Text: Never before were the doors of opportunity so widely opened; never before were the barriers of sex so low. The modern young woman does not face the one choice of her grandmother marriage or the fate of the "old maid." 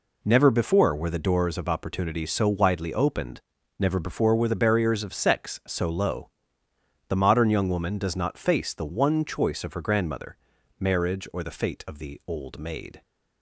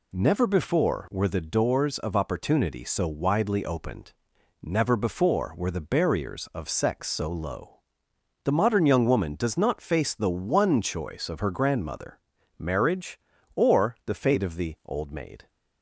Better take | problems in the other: neither | pauses between "grandmother" and "marriage"; the same in both

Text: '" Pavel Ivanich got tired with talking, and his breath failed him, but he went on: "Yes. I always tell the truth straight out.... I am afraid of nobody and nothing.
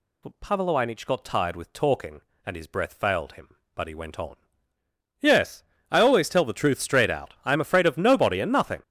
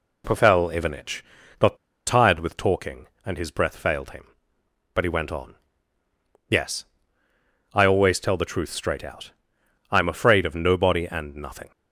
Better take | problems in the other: first | pauses between "Ivanich" and "got"; at 1.2 s; 0.38 s long // pauses between "got" and "tired"; slight; at 1.7 s; 0.29 s long

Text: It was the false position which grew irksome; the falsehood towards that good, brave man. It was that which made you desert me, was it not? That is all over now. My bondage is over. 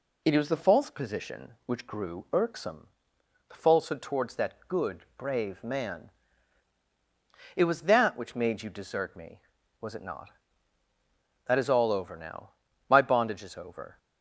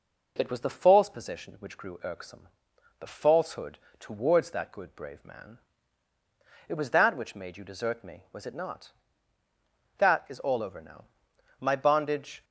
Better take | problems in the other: first | pauses between "falsehood" and "towards"; slight; at 3.7 s; 0.20 s long // stops before "is over"; at 12.4 s

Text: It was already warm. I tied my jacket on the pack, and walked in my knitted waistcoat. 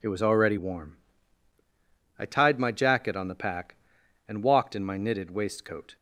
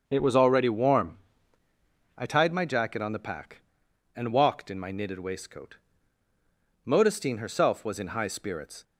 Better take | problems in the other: first | starts louder than the rest; until 1.0 s; 6.5 dB // goes on to say "Modestine herself was in high spirits"; strong; from 6.8 s on; 1.9 s long

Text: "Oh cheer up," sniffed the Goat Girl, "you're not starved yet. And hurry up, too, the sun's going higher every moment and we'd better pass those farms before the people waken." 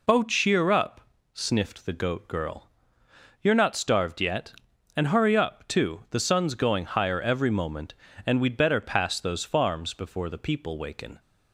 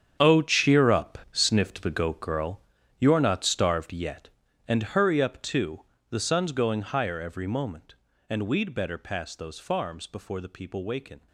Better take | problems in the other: first | gets quieter; strong; throughout; 13.5 dB

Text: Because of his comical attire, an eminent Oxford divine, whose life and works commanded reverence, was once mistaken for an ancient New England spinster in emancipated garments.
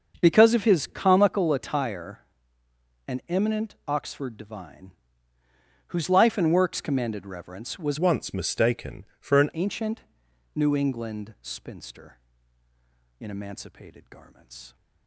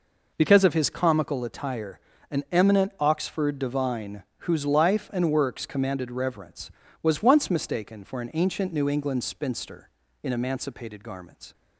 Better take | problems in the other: second | starts louder than the rest; until 1.2 s; 6 dB // changes voice from "once" to "an"; from 7.9 to 9.4 s; 1.5 s long // pauses between "ancient" and "New"; noticeable; at 10.0 s; 0.54 s long

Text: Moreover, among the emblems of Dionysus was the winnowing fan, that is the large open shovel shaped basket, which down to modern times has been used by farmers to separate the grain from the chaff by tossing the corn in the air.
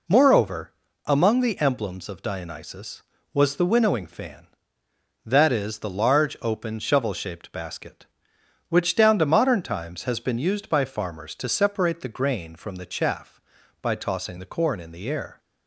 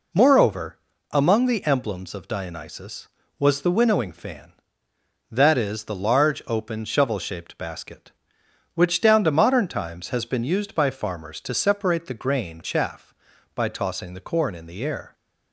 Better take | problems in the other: first | skips "from the"; at 12.6 s

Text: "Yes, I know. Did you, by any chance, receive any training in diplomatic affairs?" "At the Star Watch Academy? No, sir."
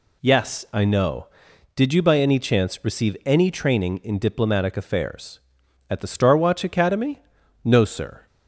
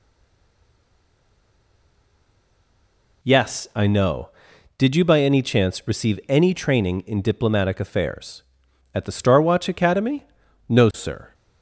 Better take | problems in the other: first | stays silent before the first word; strong; until 3.2 s; 3.2 s long

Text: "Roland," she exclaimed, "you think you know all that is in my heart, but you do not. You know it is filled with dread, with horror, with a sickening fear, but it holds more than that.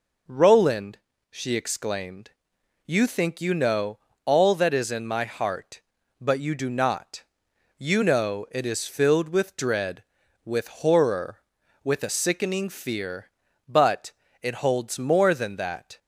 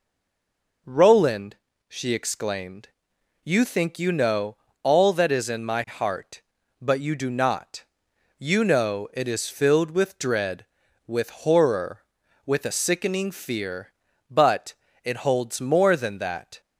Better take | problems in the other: first | stays silent before the first word; slight; until 0.8 s; 0.8 s long // pauses between "know" and "all"; slight; at 4.5 s; 0.24 s long; slight in the first // pauses between "but" and "it"; slight; at 14.7 s; 0.28 s long; slight in the first

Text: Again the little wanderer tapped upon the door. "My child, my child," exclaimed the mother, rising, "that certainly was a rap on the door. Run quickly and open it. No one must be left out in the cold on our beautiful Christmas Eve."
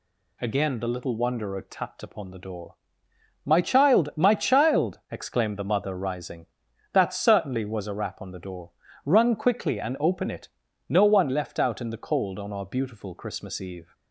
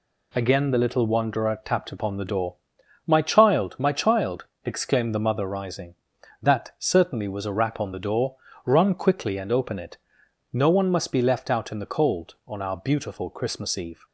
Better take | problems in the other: second | skips "must be"; at 11.2 s

